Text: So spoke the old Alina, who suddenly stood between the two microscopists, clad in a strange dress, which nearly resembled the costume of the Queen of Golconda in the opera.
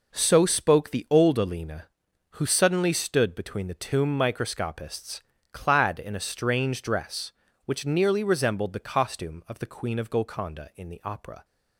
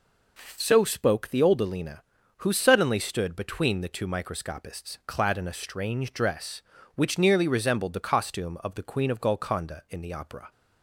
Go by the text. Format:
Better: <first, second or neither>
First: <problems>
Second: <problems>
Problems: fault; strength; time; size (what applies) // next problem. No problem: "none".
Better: second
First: says "tomb" for "two"; at 3.7 s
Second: none